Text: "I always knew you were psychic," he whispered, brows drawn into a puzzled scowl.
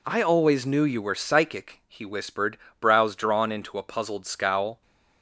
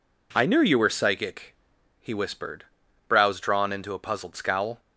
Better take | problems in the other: first | skips "always"; at 0.4 s

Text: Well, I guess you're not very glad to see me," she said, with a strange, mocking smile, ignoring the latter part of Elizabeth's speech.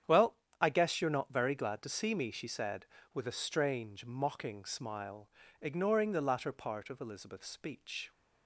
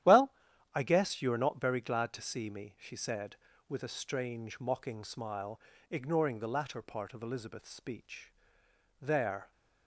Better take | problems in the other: first | starts louder than the rest; strong; until 1.4 s; 11.5 dB; strong in the first // goes on to say "There"; from 8.9 s on; 0.52 s long

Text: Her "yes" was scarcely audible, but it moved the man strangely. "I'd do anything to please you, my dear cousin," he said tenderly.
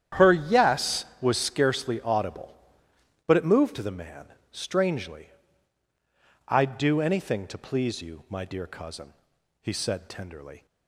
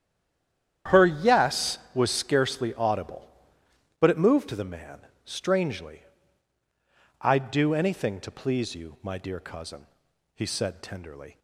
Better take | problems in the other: first | stays silent before the first word; slight; until 0.8 s; 0.8 s long // starts louder than the rest; strong; until 2.0 s; 9.5 dB; strong in the first // pauses between "man" and "strangely"; slight; at 5.0 s; 0.24 s long; slight in the first

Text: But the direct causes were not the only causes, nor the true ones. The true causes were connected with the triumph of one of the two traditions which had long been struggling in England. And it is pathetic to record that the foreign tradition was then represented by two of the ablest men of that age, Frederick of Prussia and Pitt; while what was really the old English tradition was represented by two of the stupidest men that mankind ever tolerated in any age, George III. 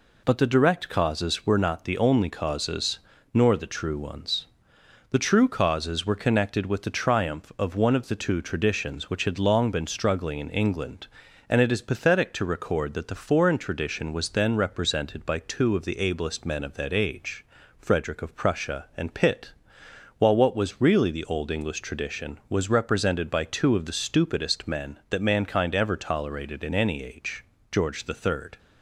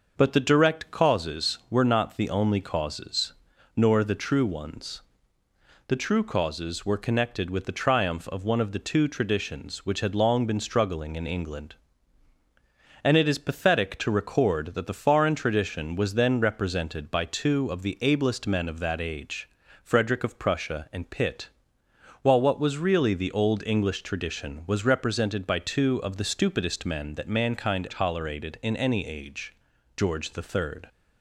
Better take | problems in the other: first | starts louder than the rest; noticeable; until 1.1 s; 6 dB // skips "ever"; at 27.8 s

